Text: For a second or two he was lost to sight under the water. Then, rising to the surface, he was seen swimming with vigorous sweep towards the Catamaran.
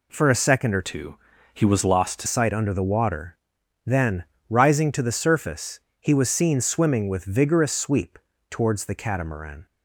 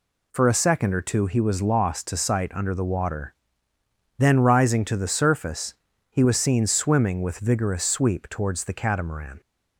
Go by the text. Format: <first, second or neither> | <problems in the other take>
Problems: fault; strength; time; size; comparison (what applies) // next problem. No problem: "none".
second | changes voice from "two" to "to"; from 0.8 to 2.2 s; 1.4 s long // pauses between "two" and "he"; at 1.1 s; 0.38 s long // pauses between "sweep" and "towards"; slight; at 8.1 s; 0.32 s long